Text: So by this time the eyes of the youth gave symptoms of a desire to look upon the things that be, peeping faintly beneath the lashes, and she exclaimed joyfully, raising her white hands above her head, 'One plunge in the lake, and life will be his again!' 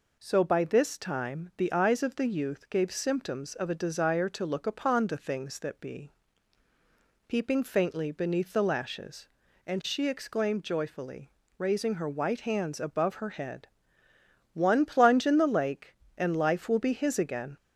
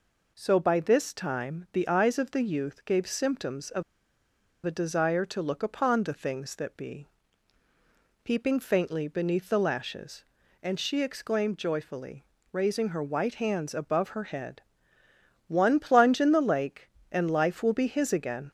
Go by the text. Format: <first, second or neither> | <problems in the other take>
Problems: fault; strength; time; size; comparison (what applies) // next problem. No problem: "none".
first | pauses between "of" and "a"; noticeable; at 3.8 s; 0.81 s long